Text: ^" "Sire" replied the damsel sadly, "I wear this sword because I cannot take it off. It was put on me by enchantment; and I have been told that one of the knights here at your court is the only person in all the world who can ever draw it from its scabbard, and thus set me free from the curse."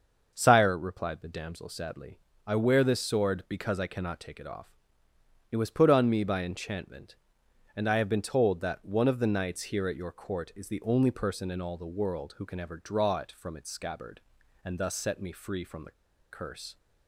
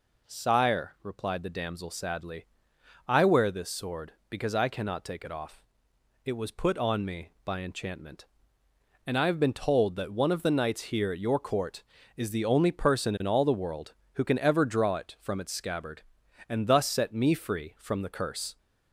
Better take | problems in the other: second | starts louder than the rest; until 1.3 s; 6.5 dB // pauses between "the" and "curse"; at 15.9 s; 0.39 s long

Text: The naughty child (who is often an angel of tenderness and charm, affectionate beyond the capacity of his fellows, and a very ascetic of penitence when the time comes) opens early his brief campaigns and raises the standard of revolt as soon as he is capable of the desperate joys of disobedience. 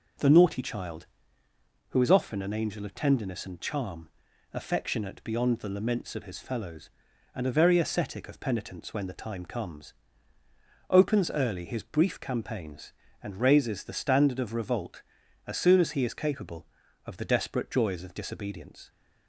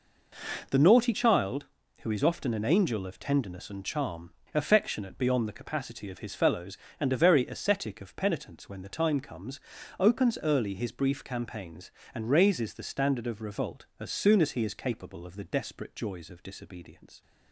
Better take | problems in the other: second | says "laments" for "capacity"; at 5.6 s

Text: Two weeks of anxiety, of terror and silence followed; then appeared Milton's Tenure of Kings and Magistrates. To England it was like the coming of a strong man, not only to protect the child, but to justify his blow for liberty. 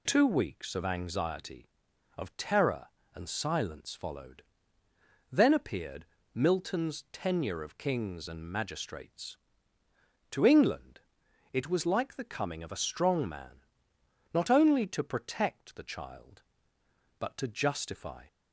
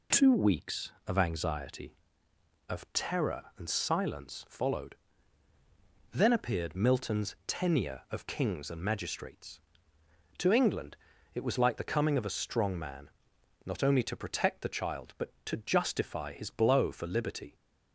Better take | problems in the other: second | pauses between "appeared" and "Milton's"; slight; at 6.0 s; 0.26 s long // pauses between "England" and "it"; noticeable; at 11.0 s; 0.52 s long; slight in the second // stops before "his blow for liberty"; at 18.2 s

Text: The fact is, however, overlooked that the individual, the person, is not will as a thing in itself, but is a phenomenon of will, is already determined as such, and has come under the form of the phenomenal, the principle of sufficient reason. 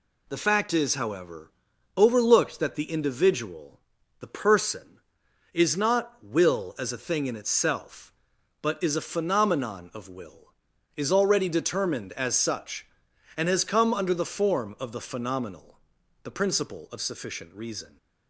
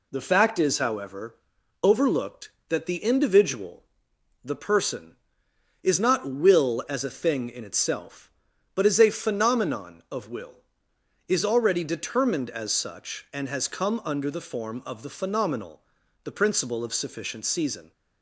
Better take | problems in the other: first | says "season" for "reason"; at 17.4 s

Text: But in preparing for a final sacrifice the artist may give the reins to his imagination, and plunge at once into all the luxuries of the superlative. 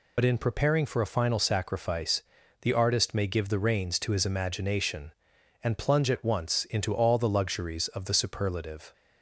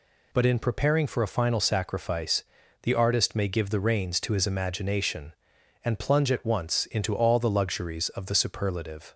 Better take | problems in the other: second | loses the start of "But"; at 0.1 s; 55 ms // pauses between "sacrifice" and "the"; at 2.2 s; 0.40 s long; also in the second

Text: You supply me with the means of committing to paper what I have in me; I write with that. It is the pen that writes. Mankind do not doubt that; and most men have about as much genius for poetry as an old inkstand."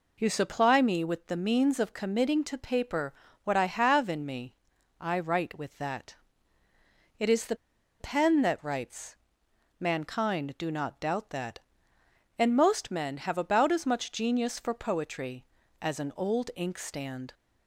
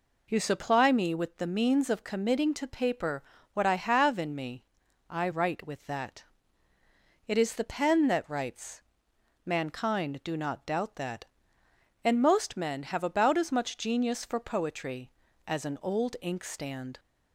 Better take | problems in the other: second | pauses between "paper" and "what"; slight; at 3.1 s; 0.32 s long; slight in the second // pauses between "the" and "pen"; at 7.5 s; 0.45 s long

